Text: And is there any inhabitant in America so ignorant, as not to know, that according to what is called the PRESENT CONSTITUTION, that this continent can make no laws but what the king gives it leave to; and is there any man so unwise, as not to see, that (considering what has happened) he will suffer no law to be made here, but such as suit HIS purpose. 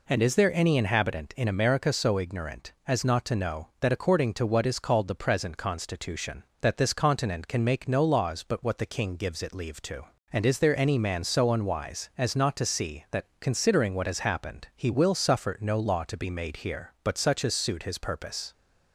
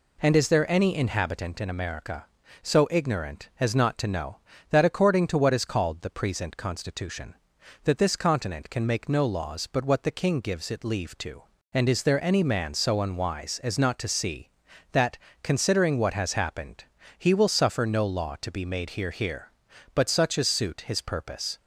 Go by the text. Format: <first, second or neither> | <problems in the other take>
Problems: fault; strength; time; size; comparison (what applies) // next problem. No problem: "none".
first | says "here" twice; at 19.1 s